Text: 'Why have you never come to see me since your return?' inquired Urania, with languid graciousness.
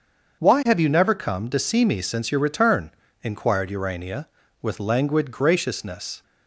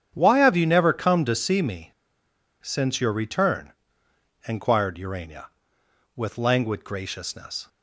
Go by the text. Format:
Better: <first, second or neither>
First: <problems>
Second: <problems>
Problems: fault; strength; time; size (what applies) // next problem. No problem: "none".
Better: first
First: starts louder than the rest; until 1.4 s; 6.5 dB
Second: starts louder than the rest; strong; until 1.1 s; 8.5 dB // pauses between "me" and "since"; noticeable; at 1.9 s; 0.71 s long